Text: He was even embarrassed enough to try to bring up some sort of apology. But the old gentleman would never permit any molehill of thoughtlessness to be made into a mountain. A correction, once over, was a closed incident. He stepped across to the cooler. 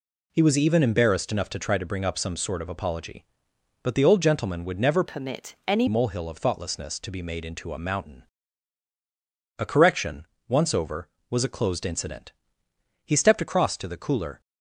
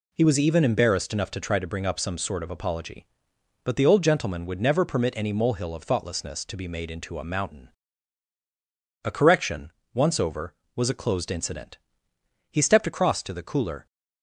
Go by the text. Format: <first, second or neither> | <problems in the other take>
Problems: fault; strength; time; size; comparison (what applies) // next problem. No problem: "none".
second | changes voice from "permit" to "any"; from 5.0 to 5.8 s; 0.8 s long